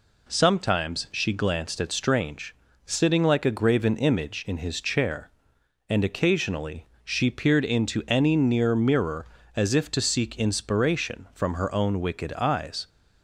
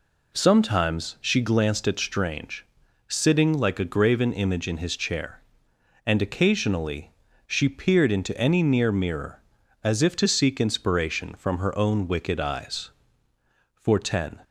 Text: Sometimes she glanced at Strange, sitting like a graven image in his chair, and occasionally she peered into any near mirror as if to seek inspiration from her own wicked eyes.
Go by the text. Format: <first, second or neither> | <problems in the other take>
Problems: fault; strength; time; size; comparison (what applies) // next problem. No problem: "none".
first | pauses between "occasionally" and "she"; slight; at 7.1 s; 0.34 s long; slight in the first // goes on to say "For ten"; noticeable; from 13.7 s on; 0.64 s long